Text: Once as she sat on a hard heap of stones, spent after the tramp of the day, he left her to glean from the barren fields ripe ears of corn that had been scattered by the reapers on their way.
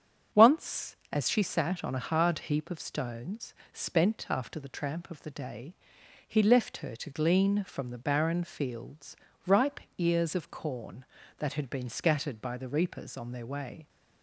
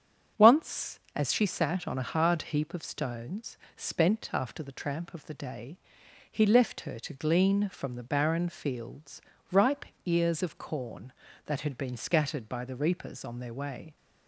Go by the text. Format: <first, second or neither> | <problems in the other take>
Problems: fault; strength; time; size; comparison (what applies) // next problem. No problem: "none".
neither | starts louder than the rest; strong; the same in both // pauses between "fields" and "ripe"; slight; the same in both // pauses between "ripe" and "ears"; slight; the same in both